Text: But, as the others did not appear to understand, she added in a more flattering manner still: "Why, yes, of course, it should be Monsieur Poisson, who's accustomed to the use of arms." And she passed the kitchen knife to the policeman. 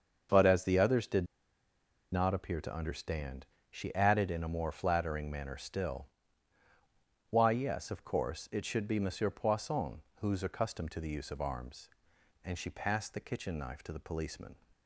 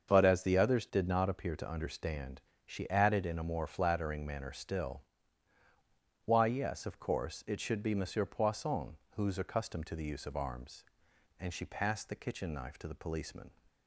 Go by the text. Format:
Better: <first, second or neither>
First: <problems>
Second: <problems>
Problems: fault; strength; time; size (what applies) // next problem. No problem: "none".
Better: second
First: starts louder than the rest; until 2.1 s; 6.5 dB // pauses between "did" and "not"; noticeable; at 1.2 s; 0.86 s long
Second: starts louder than the rest; until 1.1 s; 6.5 dB